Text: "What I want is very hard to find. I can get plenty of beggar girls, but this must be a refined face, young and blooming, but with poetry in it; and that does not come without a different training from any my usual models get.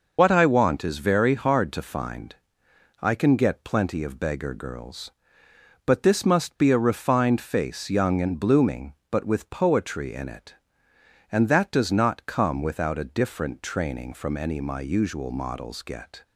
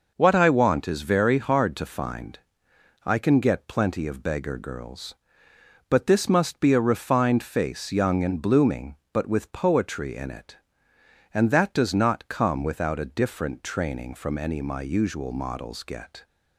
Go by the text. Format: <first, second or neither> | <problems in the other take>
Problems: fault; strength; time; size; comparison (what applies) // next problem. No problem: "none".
second | loses the start of "What"; at 0.1 s; 75 ms